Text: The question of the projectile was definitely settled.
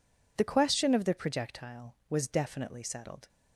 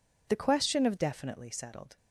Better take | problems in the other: first | skips "the projectile was"; at 0.9 s

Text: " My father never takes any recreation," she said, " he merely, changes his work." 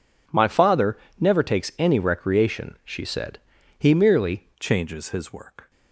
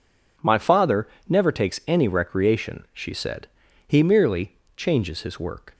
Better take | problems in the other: second | pauses between "father" and "never"; slight; at 0.9 s; 0.22 s long; slight in the second // changes voice at "changes"; from 4.6 s on; 1.1 s long

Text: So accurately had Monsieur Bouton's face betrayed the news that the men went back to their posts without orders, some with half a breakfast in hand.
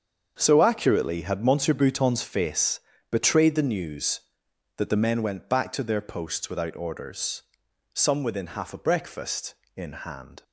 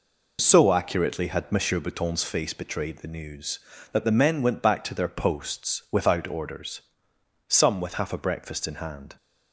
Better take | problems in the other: second | starts louder than the rest; until 1.4 s; 7 dB // pauses between "face" and "betrayed"; slight; at 2.7 s; 0.30 s long // says "within" for "with"; at 8.2 s

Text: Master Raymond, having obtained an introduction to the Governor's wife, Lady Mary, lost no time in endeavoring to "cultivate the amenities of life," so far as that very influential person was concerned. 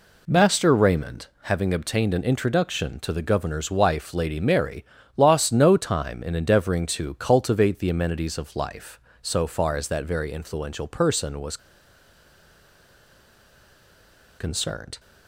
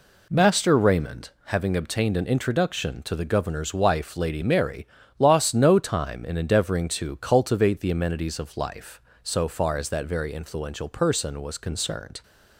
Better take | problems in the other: second | pauses between "was" and "concerned"; strong; at 11.5 s; 2.8 s long

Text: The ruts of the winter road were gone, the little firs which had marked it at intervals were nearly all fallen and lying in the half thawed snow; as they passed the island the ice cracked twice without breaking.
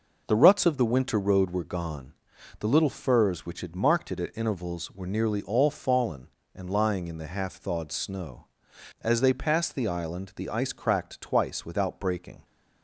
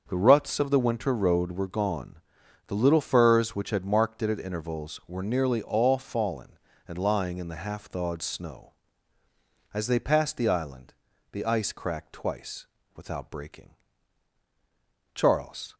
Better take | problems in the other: first | starts louder than the rest; until 1.0 s; 6.5 dB // pauses between "island" and "the"; at 10.9 s; 0.40 s long // pauses between "twice" and "without"; slight; at 12.6 s; 0.28 s long // goes on to say "Charles"; from 15.1 s on; 0.60 s long

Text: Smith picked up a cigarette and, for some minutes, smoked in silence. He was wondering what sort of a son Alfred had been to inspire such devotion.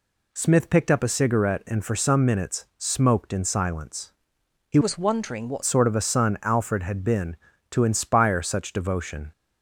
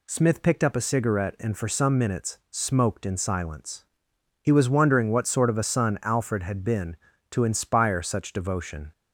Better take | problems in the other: second | changes voice from "was" to "what"; from 4.8 to 5.6 s; 0.8 s long

